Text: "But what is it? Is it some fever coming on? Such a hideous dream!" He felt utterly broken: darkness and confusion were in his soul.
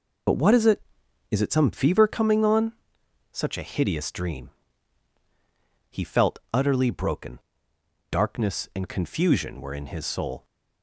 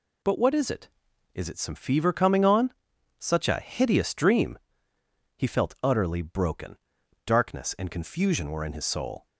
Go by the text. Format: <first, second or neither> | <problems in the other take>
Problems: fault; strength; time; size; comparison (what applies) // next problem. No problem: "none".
second | loses the start of "But"; at 0.2 s; 50 ms